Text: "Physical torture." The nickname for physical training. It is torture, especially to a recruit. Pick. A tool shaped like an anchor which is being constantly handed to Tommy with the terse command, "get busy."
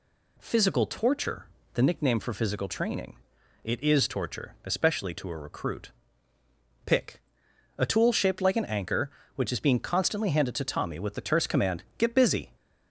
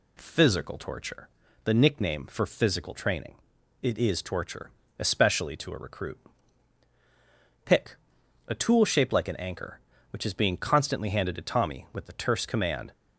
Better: first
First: none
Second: stops before "get busy"; at 12.9 s

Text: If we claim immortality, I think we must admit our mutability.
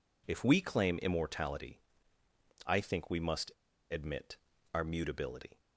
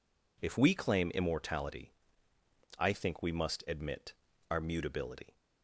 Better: second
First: pauses between "must" and "admit"; at 3.5 s; 0.38 s long // pauses between "admit" and "our"; at 4.3 s; 0.38 s long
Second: pauses between "admit" and "our"; at 4.1 s; 0.38 s long

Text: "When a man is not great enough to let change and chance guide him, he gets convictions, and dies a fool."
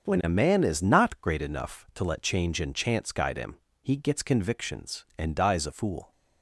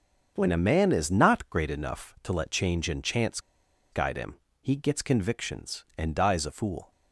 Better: first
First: starts louder than the rest; until 1.0 s; 6.5 dB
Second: starts louder than the rest; until 1.3 s; 6.5 dB // pauses between "chance" and "guide"; noticeable; at 3.3 s; 0.52 s long

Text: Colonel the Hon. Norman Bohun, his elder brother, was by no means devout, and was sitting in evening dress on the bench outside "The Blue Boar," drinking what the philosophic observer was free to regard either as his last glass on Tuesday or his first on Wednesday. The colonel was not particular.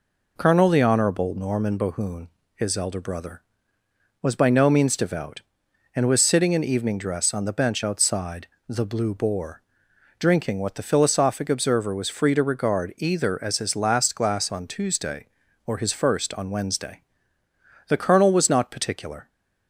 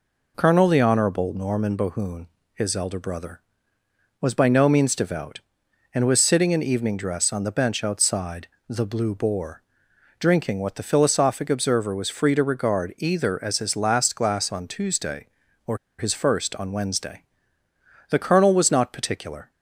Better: first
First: pauses between "outside" and "The"; slight; at 8.4 s; 0.20 s long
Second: pauses between "outside" and "The"; slight; at 8.4 s; 0.20 s long // pauses between "or" and "his"; slight; at 15.7 s; 0.20 s long

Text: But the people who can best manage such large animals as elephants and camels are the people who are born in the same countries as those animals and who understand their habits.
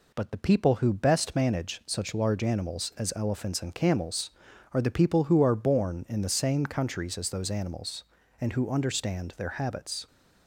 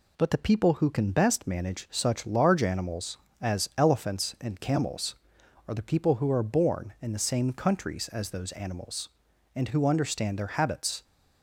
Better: second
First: skips "can"; at 0.9 s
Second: none

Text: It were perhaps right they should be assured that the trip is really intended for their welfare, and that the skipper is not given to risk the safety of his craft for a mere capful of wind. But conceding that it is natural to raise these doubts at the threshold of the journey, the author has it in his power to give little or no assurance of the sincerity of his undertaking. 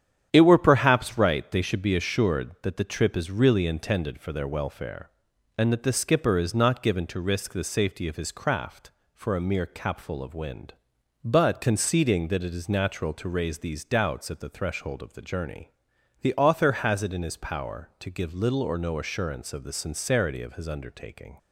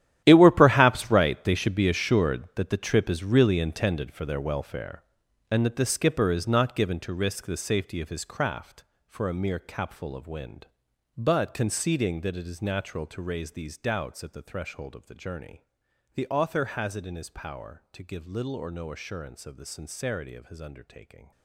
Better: first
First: starts louder than the rest; strong; until 1.3 s; 9.5 dB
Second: gets quieter; strong; throughout; 15.5 dB // starts louder than the rest; strong; until 1.2 s; 11.5 dB

